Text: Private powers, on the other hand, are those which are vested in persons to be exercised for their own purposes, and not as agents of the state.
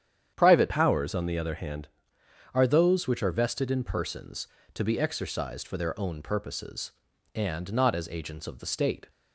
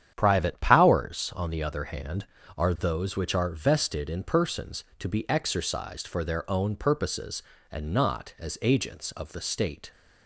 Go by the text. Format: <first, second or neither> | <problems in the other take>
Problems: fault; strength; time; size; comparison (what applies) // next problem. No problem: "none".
second | starts louder than the rest; strong; until 1.3 s; 9 dB; strong in the second // changes voice from "powers" to "hand"; from 0.6 to 1.8 s; 1.2 s long